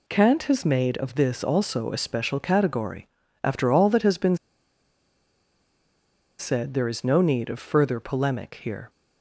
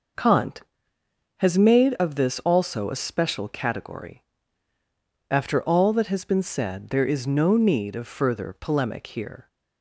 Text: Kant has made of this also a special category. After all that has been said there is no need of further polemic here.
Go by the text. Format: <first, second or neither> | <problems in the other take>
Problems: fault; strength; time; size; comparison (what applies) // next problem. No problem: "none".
second | pauses between "been" and "said"; strong; at 4.3 s; 2.0 s long